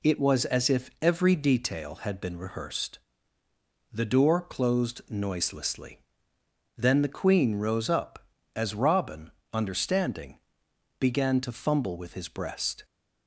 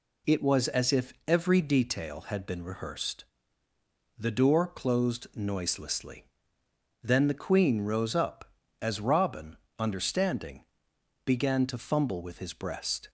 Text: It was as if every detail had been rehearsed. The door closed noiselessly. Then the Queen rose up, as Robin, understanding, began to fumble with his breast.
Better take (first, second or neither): neither